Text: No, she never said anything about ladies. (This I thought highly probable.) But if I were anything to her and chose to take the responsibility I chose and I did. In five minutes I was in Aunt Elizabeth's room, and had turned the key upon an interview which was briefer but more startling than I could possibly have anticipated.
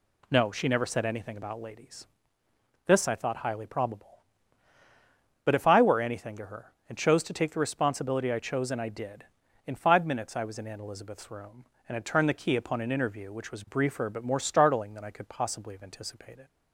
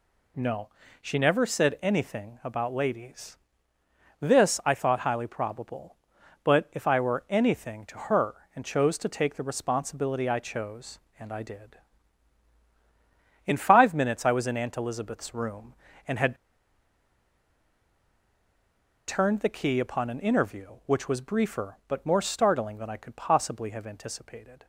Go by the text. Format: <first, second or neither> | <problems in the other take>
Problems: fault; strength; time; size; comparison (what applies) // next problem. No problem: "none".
first | pauses between "had" and "turned"; strong; at 16.3 s; 2.7 s long